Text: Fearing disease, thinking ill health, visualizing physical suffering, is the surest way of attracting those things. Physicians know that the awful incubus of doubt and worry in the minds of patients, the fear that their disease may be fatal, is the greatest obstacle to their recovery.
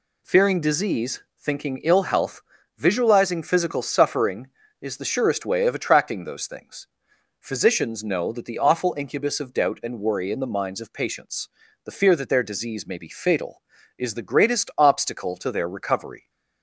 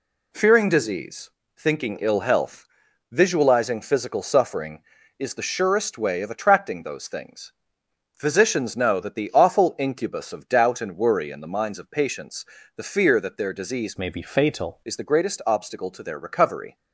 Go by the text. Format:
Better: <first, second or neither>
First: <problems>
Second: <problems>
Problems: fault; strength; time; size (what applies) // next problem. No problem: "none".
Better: first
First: none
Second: changes voice from "may" to "fatal"; from 13.9 to 14.8 s; 0.9 s long